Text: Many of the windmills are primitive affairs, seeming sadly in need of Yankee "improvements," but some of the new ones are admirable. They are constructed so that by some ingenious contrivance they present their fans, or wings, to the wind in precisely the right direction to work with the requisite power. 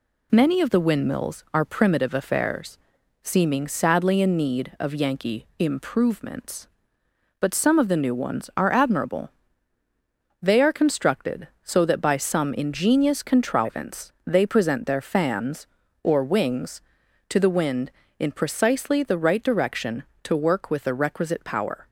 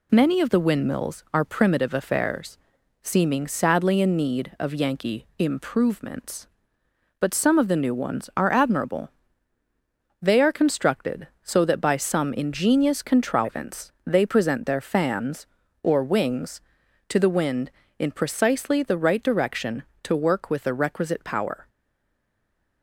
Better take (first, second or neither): first